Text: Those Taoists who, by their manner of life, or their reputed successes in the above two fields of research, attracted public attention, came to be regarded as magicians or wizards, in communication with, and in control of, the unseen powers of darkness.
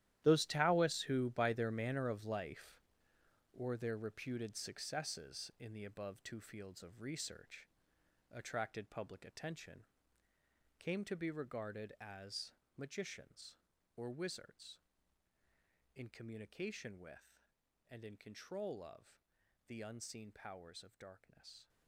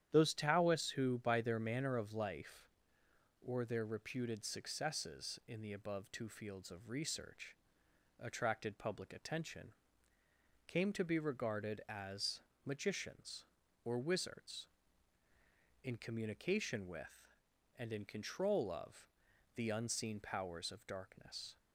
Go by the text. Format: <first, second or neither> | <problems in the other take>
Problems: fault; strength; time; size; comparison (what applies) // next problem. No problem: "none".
second | gets quieter; strong; throughout; 14 dB // starts louder than the rest; strong; until 1.2 s; 12.5 dB; strong in the second // pauses between "as" and "magicians"; slight; at 12.5 s; 0.24 s long; slight in the second